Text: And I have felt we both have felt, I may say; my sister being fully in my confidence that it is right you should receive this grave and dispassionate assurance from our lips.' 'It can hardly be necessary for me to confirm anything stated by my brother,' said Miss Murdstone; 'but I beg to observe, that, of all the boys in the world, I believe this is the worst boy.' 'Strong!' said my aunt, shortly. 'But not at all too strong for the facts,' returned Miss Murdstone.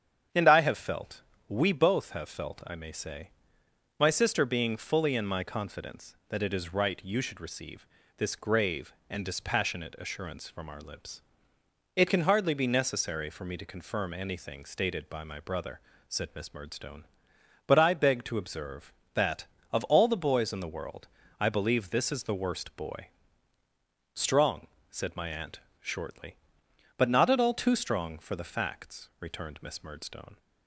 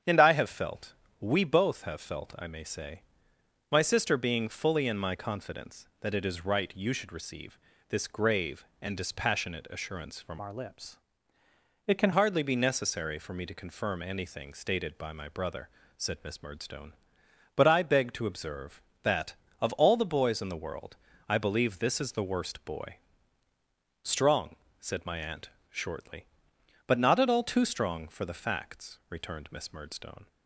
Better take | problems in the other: first | starts louder than the rest; strong; until 1.3 s; 8 dB; strong in the first // pauses between "felt" and "we"; slight; at 0.9 s; 0.26 s long; slight in the first // pauses between "receive" and "this"; slight; at 7.5 s; 0.34 s long; slight in the first // changes voice from "our" to "can"; from 10.4 to 12.1 s; 1.7 s long

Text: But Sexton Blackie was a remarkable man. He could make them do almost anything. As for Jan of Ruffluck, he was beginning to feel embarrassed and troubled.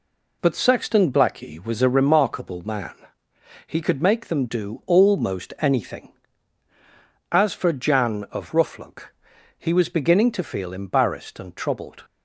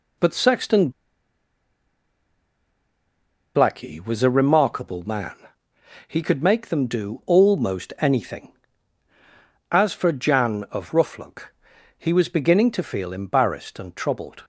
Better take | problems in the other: first | pauses between "Sexton" and "Blackie"; strong; at 0.9 s; 2.6 s long

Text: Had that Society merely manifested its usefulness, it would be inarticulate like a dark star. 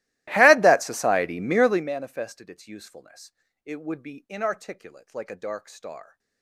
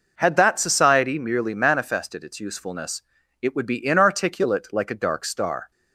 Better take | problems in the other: second | starts louder than the rest; strong; until 1.9 s; 17.5 dB

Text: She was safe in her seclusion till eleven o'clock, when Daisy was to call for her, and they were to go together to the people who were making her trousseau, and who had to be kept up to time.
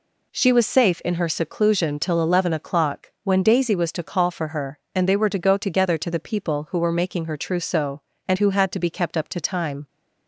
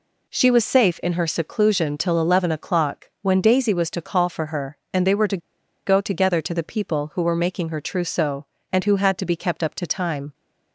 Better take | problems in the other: first | pauses between "to" and "go"; noticeable; at 5.3 s; 0.48 s long

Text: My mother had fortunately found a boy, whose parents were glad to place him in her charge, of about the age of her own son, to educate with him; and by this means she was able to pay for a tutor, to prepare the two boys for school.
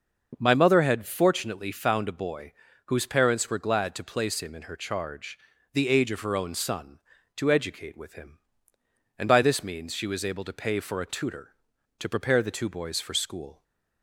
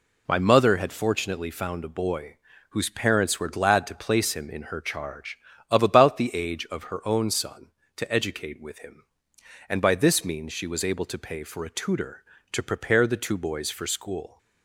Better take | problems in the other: second | starts louder than the rest; noticeable; until 1.4 s; 6 dB // skips "of about"; at 5.5 s

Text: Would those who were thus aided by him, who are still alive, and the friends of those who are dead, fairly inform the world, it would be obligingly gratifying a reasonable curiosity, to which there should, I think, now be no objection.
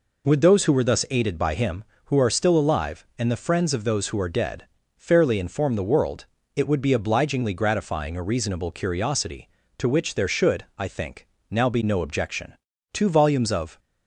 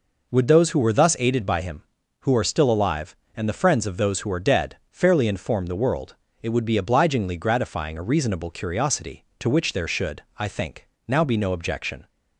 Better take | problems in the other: second | goes on to say "Two volumes of"; noticeable; from 12.9 s on; 0.86 s long

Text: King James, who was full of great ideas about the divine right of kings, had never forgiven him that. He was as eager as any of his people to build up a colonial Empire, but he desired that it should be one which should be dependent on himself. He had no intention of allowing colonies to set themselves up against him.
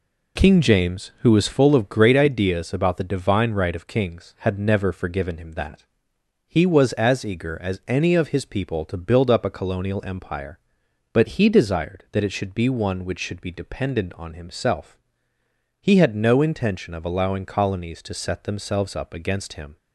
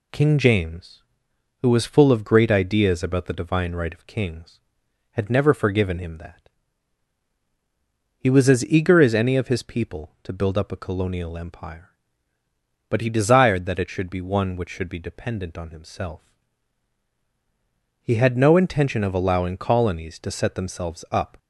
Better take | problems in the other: first | stops before "against him"; at 21.3 s

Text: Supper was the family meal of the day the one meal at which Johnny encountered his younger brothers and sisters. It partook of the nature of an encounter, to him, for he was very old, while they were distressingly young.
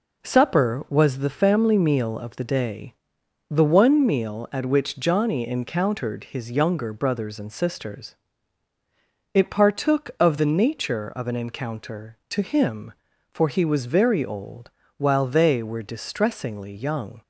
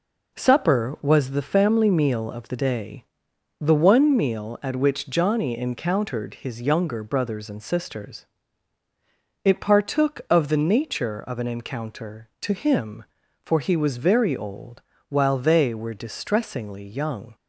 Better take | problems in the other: neither | pauses between "day" and "the"; noticeable; the same in both

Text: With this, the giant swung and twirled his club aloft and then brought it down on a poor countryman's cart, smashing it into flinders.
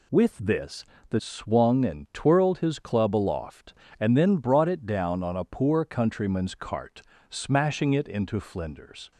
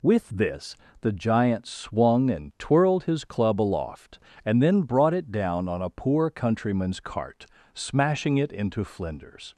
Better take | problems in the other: second | skips "giant"; at 1.2 s

